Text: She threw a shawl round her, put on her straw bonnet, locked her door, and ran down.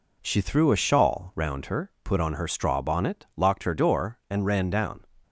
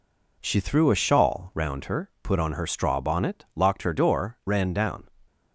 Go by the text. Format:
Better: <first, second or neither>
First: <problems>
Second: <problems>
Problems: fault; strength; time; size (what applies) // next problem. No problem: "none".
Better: first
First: none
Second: skips "and"; at 4.4 s